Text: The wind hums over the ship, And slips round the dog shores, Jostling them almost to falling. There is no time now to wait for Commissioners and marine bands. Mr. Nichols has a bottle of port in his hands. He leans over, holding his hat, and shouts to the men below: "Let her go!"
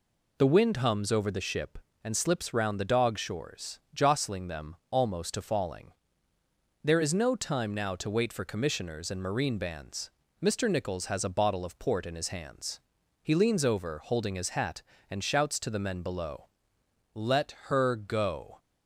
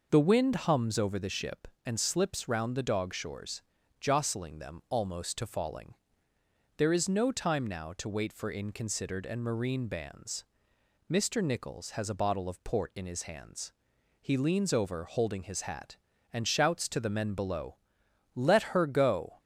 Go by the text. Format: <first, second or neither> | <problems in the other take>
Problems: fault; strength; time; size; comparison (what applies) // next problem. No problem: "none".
first | says "Inconsidered" for "Commissioners"; at 8.5 s